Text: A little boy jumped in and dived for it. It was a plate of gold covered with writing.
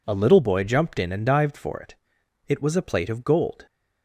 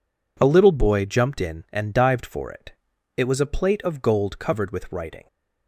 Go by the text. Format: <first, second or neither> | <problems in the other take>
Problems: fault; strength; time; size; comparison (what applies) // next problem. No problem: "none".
second | stops before "covered with writing"; at 3.6 s